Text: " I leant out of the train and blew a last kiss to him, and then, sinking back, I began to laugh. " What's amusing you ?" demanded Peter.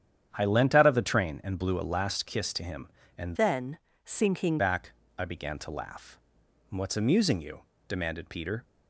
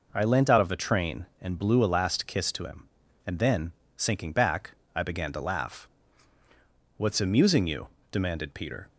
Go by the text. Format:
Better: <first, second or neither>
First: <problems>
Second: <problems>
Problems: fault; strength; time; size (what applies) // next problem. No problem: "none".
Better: second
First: starts louder than the rest; strong; until 1.3 s; 9.5 dB // changes voice from "then" to "sinking"; from 3.3 to 4.5 s; 1.2 s long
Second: none